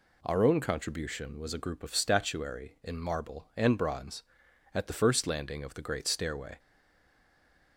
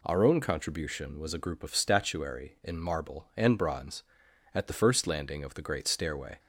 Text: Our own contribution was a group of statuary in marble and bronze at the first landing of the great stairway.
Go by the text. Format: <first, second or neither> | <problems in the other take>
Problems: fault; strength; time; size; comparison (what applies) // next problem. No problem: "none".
second | stays silent after the last word; noticeable; from 6.5 s on; 1.2 s long